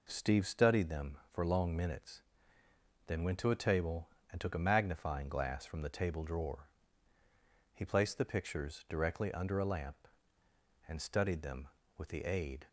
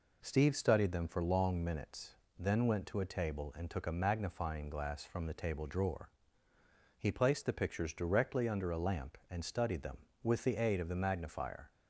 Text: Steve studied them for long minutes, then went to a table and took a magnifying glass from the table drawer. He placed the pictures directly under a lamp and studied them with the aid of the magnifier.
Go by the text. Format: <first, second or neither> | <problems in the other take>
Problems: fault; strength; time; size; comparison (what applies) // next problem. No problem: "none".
second | stops before "of the magnifier"; at 12.6 s